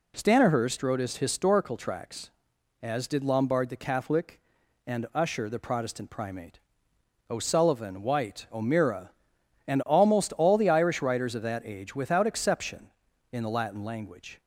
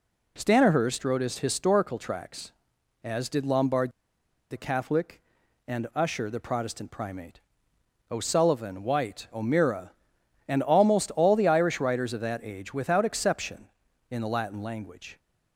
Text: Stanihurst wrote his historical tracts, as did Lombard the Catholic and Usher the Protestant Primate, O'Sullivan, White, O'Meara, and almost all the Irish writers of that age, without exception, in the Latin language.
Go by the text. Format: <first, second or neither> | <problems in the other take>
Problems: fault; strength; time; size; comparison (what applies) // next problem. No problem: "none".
first | pauses between "Lombard" and "the"; noticeable; at 3.8 s; 0.61 s long